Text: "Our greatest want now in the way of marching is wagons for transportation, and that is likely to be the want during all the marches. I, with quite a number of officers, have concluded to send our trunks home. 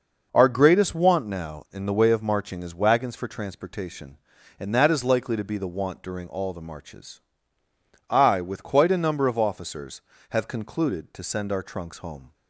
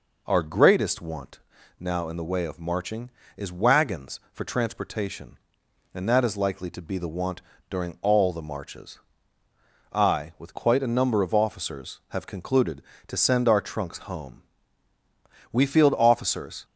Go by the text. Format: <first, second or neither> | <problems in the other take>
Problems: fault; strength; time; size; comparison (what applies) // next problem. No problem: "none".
first | pauses between "want" and "now"; at 1.3 s; 0.40 s long // pauses between "want" and "during"; slight; at 7.4 s; 0.27 s long // goes on to say "We field officers"; noticeable; from 15.5 s on; 1.1 s long